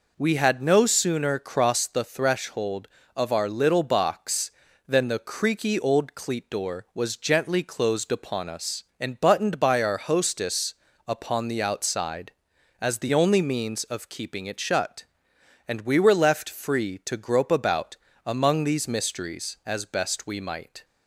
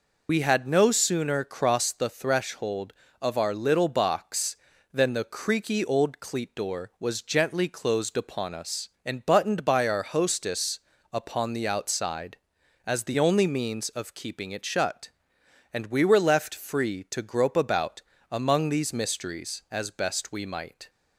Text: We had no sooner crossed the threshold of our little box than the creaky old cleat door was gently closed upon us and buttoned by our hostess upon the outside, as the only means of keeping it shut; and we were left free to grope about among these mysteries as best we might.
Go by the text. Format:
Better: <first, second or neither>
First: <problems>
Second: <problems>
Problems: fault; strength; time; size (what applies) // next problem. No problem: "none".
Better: first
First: pauses between "hostess" and "upon"; slight; at 10.7 s; 0.34 s long // pauses between "about" and "among"; slight; at 17.9 s; 0.28 s long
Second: loses the start of "We"; at 0.2 s; 80 ms // pauses between "hostess" and "upon"; slight; at 10.7 s; 0.34 s long // pauses between "about" and "among"; slight; at 18.0 s; 0.28 s long